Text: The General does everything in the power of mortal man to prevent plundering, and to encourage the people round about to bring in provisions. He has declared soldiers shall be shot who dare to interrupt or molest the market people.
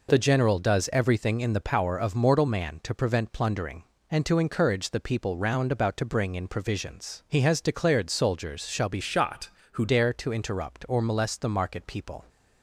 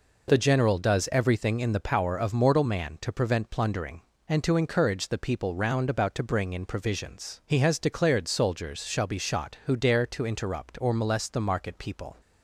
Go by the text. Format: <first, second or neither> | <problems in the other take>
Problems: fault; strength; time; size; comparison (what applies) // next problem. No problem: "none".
second | changes voice from "shot" to "who"; from 9.0 to 9.8 s; 0.8 s long